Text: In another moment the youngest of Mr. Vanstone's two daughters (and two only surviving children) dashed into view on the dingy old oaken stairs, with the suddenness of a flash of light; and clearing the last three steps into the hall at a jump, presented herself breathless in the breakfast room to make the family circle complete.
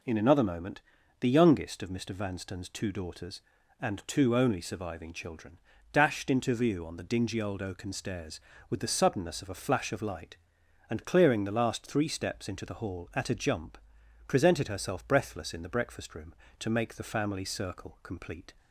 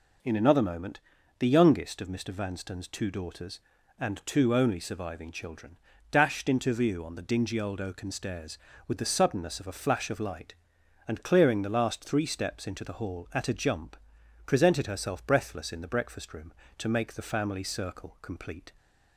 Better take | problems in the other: neither | pauses between "moment" and "the"; the same in both

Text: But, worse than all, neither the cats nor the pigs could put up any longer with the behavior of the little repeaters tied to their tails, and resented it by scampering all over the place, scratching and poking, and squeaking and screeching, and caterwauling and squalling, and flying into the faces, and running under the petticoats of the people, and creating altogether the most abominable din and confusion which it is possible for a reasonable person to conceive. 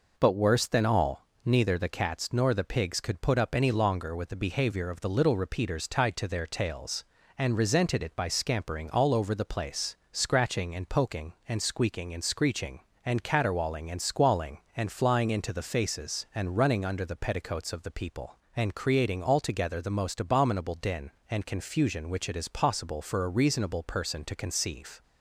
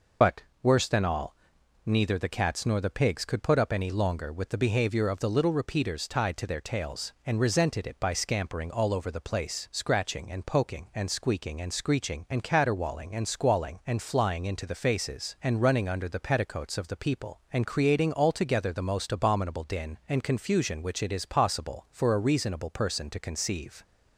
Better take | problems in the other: first | loses the start of "But"; at 0.2 s; 55 ms

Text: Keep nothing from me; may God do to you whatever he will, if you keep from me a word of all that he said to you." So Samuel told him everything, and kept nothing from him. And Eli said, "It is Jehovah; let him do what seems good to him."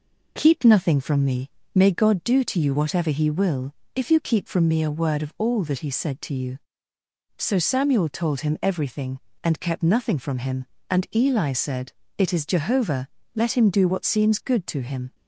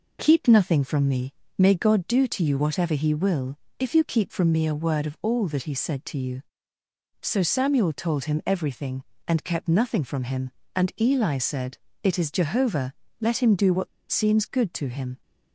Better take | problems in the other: first | pauses between "what" and "seems"; slight; at 13.8 s; 0.24 s long

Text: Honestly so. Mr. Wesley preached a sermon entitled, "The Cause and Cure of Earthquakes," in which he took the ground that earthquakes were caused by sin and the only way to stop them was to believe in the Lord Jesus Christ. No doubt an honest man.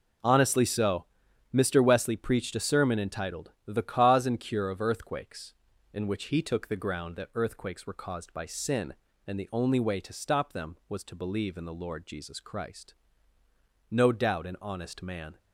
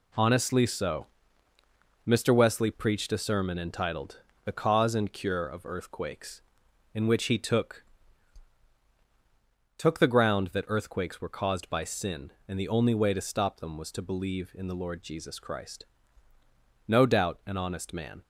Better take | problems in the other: first | says "took" twice; at 9.7 s

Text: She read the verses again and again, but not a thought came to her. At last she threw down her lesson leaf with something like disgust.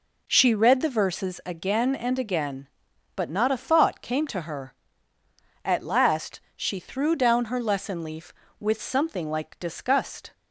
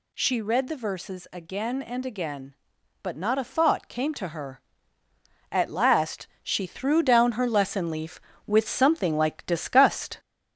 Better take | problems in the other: first | gets louder; slight; throughout; 3 dB // pauses between "last" and "she"; slight; at 6.2 s; 0.16 s long; slight in the first

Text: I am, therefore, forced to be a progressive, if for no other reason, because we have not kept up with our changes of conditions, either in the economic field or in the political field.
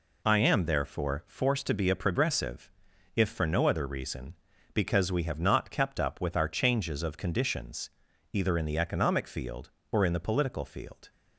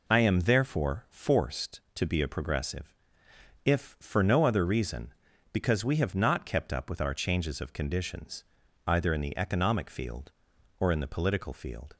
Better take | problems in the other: neither | none

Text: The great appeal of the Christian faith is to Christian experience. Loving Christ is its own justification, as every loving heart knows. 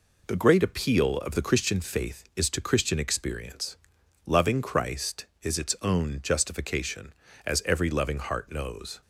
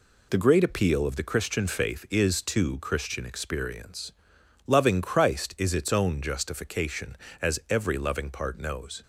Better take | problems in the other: first | says "part" for "heart"; at 8.2 s

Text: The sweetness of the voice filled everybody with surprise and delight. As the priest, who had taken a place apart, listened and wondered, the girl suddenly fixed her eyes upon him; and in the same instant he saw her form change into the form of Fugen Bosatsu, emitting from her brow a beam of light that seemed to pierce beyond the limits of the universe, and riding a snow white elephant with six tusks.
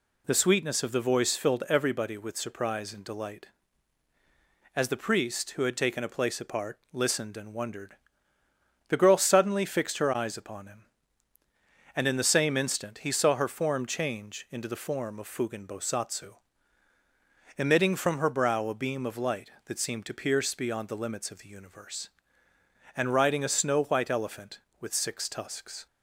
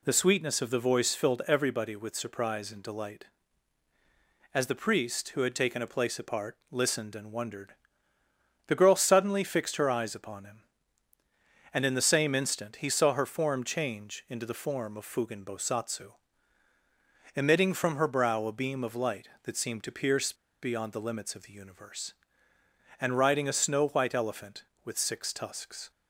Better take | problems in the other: first | pauses between "pierce" and "beyond"; slight; at 20.3 s; 0.28 s long

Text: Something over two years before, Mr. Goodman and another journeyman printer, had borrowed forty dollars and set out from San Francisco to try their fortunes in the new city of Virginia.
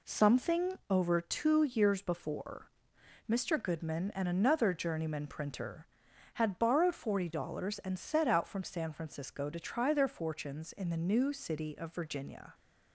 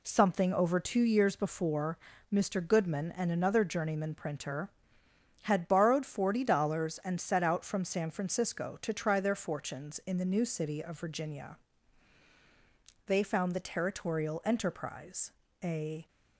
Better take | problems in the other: first | goes on to say "They found the Territorial Enterprise a"; strong; from 13.0 s on; 3.0 s long

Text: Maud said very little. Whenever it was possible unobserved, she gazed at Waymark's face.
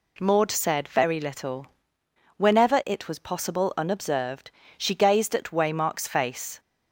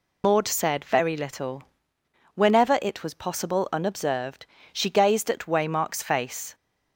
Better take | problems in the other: first | loses the start of "Maud"; at 0.2 s; 115 ms

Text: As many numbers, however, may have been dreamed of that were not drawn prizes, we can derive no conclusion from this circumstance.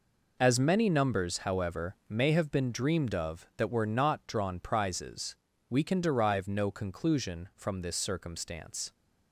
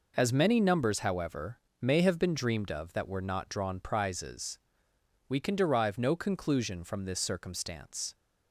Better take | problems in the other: neither | none

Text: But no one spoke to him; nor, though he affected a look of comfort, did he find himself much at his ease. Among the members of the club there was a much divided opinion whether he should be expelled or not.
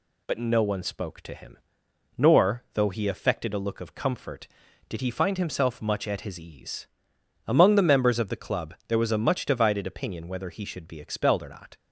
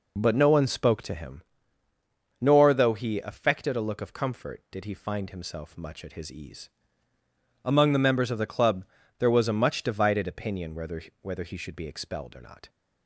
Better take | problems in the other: first | pauses between "club" and "there"; slight; at 8.8 s; 0.32 s long // says "whether" twice; at 11.2 s

